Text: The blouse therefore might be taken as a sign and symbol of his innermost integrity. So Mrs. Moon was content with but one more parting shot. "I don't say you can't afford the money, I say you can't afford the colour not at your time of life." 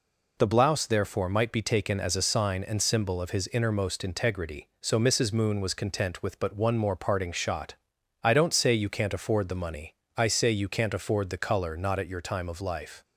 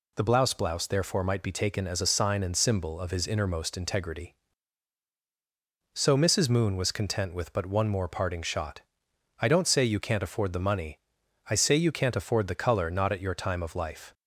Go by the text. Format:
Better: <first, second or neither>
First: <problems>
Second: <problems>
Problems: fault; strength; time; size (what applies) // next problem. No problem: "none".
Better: first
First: none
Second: says "blouse" twice; at 0.5 s